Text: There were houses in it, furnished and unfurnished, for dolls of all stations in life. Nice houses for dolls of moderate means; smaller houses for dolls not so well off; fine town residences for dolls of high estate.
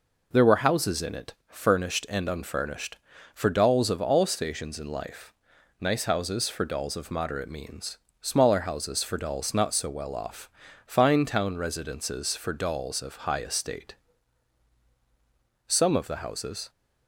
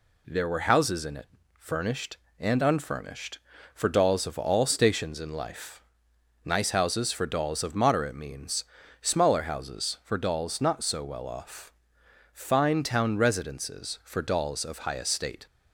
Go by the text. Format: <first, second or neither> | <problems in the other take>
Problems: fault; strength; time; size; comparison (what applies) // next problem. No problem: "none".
second | goes on to say "Some of the houses"; noticeable; from 15.6 s on; 1.0 s long